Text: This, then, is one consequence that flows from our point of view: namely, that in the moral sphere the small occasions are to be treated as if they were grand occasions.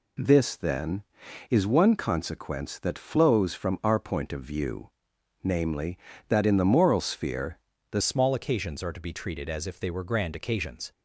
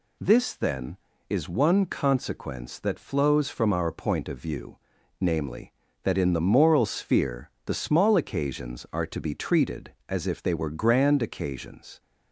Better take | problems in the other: second | pauses between "sphere" and "the"; slight; at 7.5 s; 0.34 s long; slight in the second // changes voice at "small"; from 8.0 s on; 2.9 s long

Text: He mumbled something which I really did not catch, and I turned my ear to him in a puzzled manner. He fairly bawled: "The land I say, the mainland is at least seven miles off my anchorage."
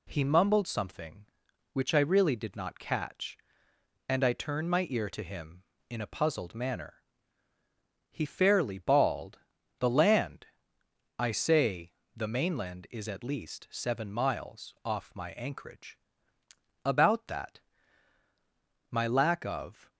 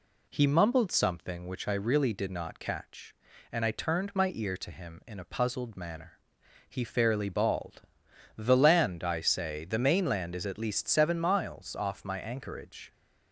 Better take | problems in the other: second | pauses between "land" and "I"; noticeable; at 10.4 s; 0.72 s long // goes on to say "About that My lack of"; strong; from 16.8 s on; 3.0 s long

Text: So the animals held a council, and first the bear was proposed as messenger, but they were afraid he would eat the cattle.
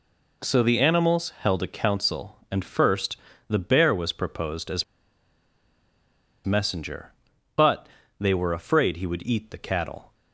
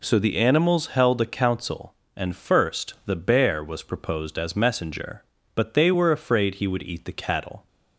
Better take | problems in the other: second | pauses between "first" and "the"; slight; at 3.1 s; 0.32 s long // pauses between "as" and "messenger"; strong; at 4.8 s; 1.6 s long // pauses between "but" and "they"; slight; at 7.8 s; 0.30 s long

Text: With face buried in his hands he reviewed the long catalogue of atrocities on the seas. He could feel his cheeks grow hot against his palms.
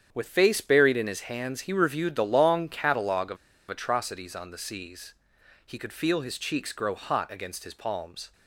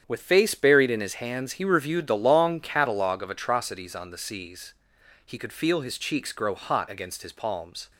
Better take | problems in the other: second | starts louder than the rest; strong; until 1.1 s; 8.5 dB; strong in the second // pauses between "of" and "atrocities"; slight; at 3.3 s; 0.33 s long

